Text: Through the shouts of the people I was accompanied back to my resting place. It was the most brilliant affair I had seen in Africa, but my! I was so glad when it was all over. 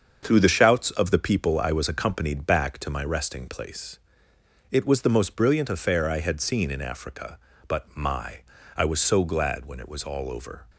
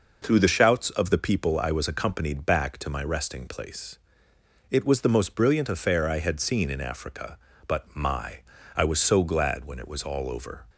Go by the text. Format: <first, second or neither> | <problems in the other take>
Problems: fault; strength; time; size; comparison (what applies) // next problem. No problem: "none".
second | gets quieter; noticeable; throughout; 6 dB